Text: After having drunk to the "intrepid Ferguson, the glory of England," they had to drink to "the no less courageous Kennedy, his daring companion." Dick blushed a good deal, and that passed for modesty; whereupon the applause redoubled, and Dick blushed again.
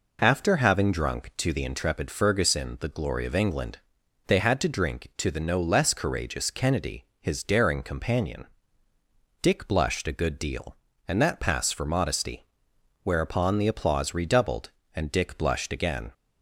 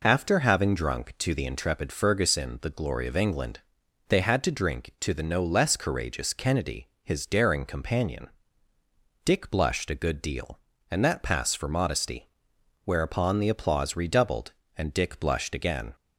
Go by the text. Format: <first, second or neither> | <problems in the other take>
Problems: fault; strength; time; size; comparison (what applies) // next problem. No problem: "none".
neither | none